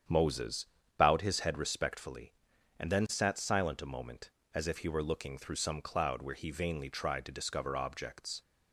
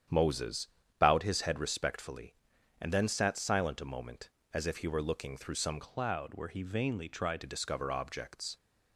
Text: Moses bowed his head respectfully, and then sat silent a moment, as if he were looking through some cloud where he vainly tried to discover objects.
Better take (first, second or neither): first